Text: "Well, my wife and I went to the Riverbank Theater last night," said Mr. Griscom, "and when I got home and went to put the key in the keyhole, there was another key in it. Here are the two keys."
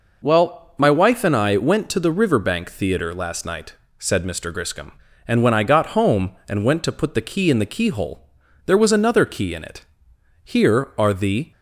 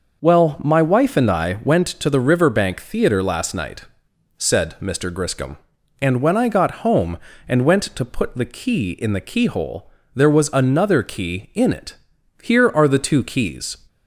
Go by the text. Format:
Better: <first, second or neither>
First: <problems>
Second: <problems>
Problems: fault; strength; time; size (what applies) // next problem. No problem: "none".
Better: second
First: stops before "two keys"; at 11.5 s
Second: none